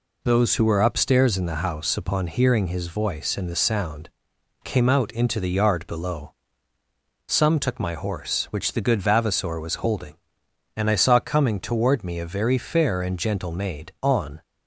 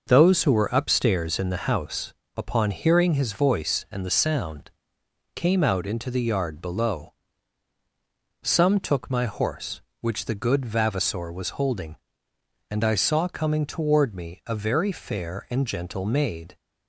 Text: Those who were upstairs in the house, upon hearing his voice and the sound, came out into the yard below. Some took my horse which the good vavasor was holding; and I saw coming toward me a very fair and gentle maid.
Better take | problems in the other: second | goes on to say "On"; slight; from 13.9 s on; 0.42 s long

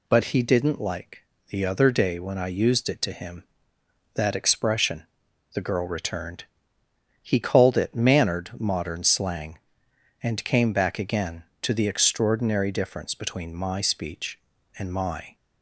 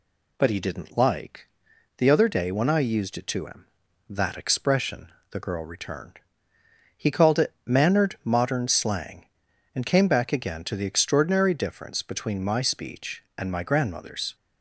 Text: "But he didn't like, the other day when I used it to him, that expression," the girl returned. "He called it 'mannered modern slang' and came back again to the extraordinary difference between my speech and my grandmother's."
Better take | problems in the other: second | stops before "grandmother's"; at 15.3 s

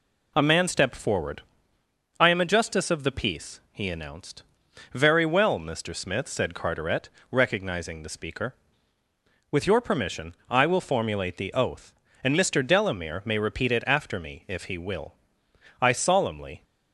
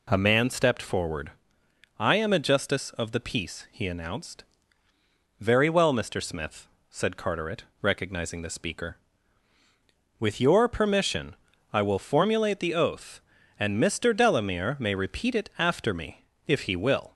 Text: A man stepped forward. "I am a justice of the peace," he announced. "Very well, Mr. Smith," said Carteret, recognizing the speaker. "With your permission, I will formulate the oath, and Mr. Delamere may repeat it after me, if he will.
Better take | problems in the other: second | goes on to say "I solemnly"; noticeable; from 15.7 s on; 0.84 s long

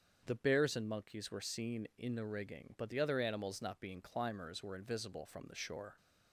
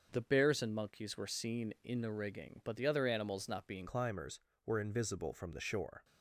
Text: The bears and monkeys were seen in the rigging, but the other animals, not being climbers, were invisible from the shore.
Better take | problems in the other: first | starts louder than the rest; until 1.1 s; 6 dB; strong in the first // changes voice at "climbers"; from 3.8 s on; 2.2 s long

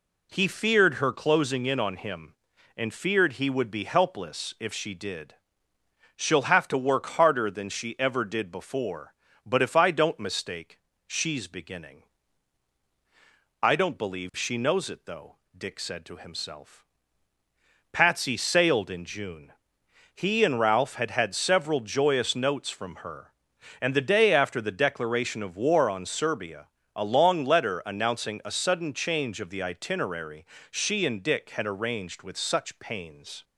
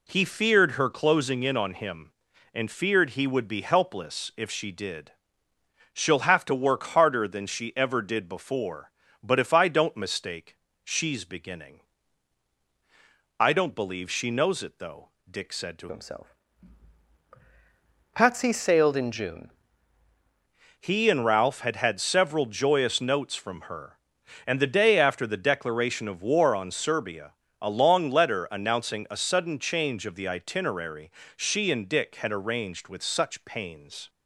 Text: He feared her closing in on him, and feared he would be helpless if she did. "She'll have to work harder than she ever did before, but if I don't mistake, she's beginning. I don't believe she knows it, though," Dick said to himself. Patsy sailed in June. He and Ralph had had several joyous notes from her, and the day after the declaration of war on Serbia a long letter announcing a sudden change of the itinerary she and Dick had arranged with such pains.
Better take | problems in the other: first | changes voice from "himself" to "June"; from 15.9 to 19.5 s; 3.6 s long // pauses between "Serbia" and "a"; slight; at 27.3 s; 0.26 s long; slight in the first // pauses between "itinerary" and "she"; slight; at 31.1 s; 0.24 s long; slight in the first

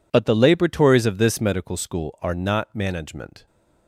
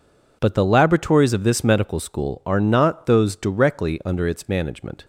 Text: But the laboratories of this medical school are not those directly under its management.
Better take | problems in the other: second | skips "those directly under its"; at 2.7 s

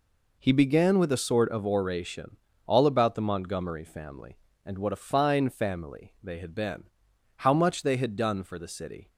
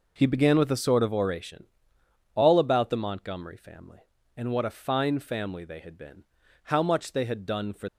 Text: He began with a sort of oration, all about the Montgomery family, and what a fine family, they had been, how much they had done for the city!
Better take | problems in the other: first | stops before "the city"; at 7.8 s

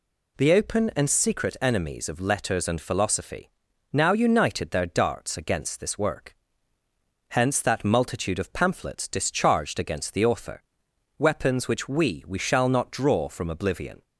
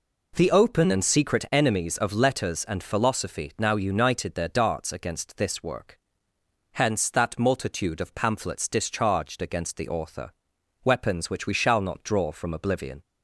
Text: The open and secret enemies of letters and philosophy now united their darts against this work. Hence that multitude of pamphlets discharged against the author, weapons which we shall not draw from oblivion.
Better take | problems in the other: second | pauses between "philosophy" and "now"; at 3.5 s; 0.40 s long // says "we" twice; at 12.2 s

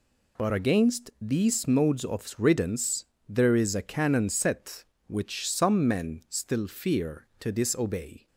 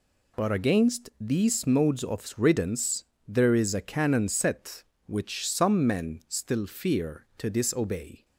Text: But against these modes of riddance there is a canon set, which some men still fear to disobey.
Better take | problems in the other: neither | pauses between "riddance" and "there"; slight; the same in both

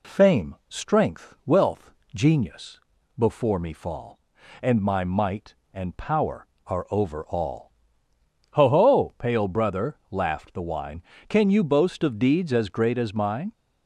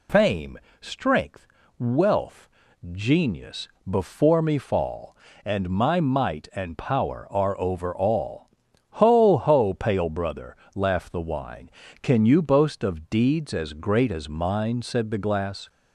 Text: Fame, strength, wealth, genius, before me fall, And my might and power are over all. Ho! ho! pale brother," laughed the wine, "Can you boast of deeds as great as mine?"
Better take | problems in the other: first | goes on to say "Said the glass"; noticeable; from 14.8 s on; 0.88 s long

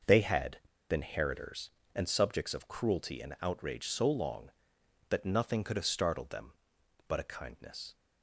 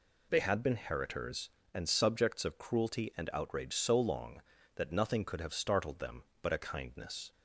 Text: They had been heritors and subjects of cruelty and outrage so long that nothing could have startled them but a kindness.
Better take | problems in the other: second | pauses between "had" and "been"; slight; at 0.5 s; 0.30 s long

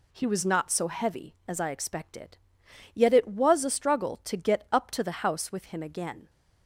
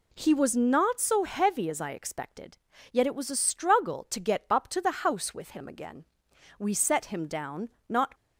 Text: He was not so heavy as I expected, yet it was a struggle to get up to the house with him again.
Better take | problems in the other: first | goes on to say "We set him down not"; from 6.5 s on; 1.5 s long

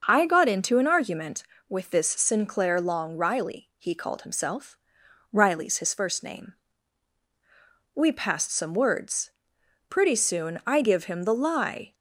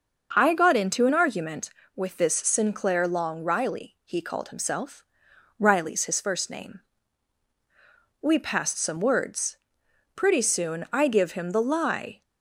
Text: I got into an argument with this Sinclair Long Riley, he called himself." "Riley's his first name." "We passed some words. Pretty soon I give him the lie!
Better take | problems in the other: neither | starts louder than the rest; noticeable; the same in both

